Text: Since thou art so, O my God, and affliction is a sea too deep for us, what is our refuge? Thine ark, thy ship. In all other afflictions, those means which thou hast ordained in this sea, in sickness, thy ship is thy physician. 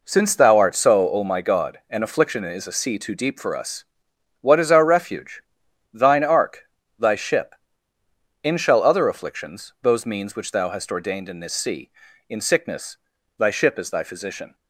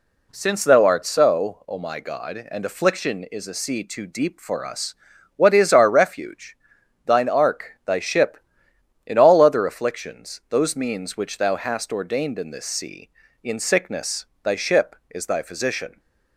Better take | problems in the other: second | says "shall" for "all"; at 8.5 s

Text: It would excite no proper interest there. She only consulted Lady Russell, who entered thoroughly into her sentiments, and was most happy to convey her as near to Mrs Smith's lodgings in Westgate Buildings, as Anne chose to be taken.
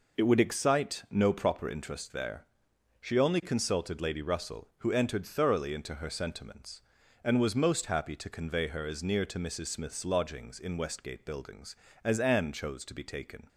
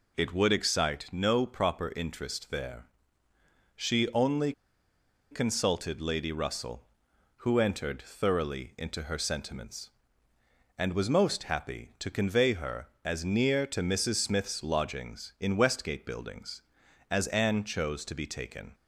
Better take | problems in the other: first | pauses between "only" and "consulted"; noticeable; at 4.5 s; 0.79 s long

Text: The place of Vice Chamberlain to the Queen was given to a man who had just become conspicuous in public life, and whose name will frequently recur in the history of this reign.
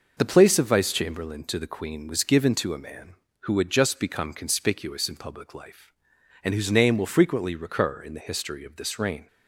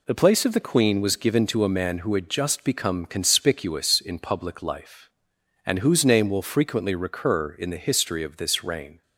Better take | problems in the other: first | skips "Vice Chamberlain to"; at 0.5 s

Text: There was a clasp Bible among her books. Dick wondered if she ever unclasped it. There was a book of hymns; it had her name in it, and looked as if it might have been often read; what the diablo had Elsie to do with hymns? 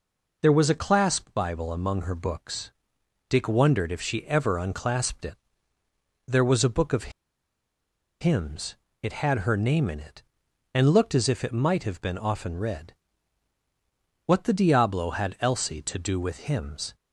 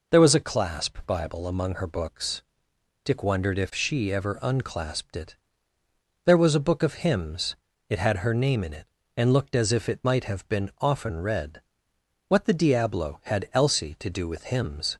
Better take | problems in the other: second | pauses between "of" and "hymns"; at 7.1 s; 1.1 s long

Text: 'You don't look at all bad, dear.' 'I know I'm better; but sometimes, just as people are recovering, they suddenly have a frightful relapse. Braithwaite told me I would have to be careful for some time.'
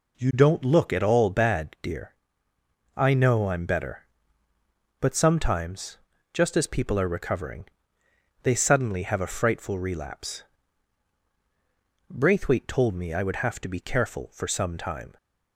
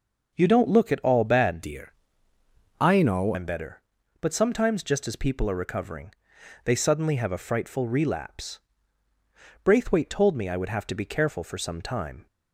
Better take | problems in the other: first | changes voice from "dear" to "know"; from 1.6 to 3.3 s; 1.7 s long

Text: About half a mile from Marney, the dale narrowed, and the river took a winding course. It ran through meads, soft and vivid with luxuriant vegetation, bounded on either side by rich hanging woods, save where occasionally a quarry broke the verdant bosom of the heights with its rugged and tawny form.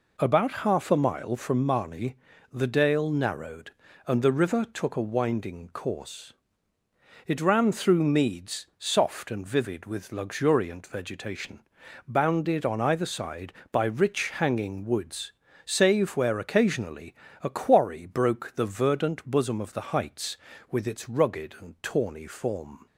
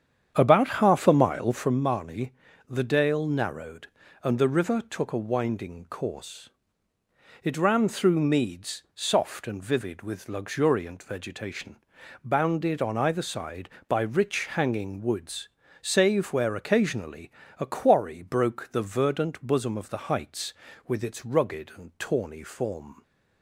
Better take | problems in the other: first | starts louder than the rest; strong; until 1.8 s; 8.5 dB // pauses between "occasionally" and "a"; slight; at 17.3 s; 0.26 s long; slight in the first

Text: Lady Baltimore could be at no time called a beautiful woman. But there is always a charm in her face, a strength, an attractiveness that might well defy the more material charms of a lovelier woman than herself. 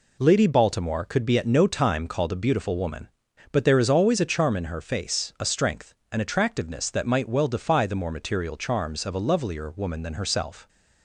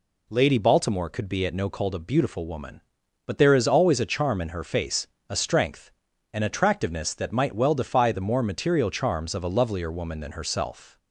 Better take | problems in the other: first | skips "time"; at 1.6 s

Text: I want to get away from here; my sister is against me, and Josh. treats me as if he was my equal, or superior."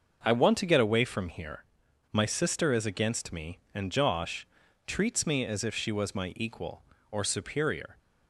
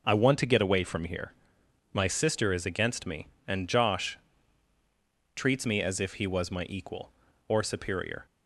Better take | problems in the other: second | starts louder than the rest; until 1.2 s; 6 dB // says "she" for "he"; at 5.7 s

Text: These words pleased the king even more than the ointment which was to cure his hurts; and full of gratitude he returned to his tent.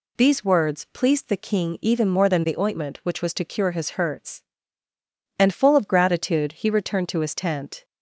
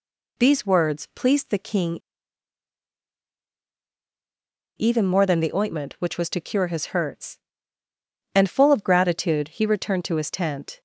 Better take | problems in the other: first | pauses between "king" and "even"; strong; at 2.0 s; 2.7 s long

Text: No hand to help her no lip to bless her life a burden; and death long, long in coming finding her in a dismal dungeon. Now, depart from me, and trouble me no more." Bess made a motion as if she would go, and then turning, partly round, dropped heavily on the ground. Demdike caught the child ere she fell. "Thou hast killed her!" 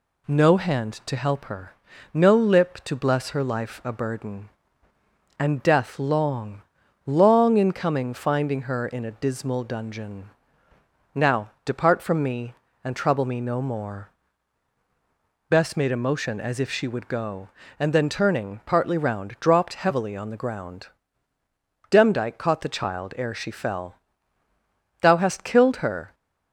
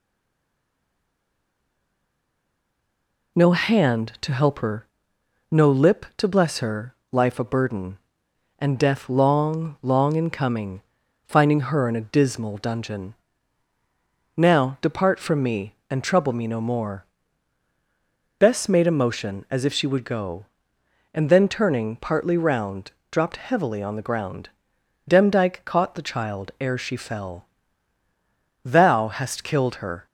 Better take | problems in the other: first | stays silent before the first word; strong; until 3.3 s; 3.3 s long // pauses between "her" and "no"; noticeable; at 4.8 s; 0.64 s long; also in the first // pauses between "her" and "life"; slight; at 6.9 s; 0.18 s long // pauses between "coming" and "finding"; noticeable; at 10.8 s; 0.46 s long

